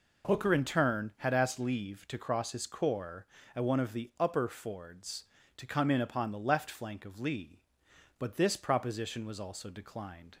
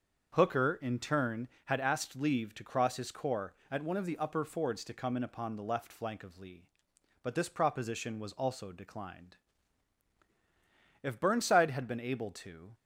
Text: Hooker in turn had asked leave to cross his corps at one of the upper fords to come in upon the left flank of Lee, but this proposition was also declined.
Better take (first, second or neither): first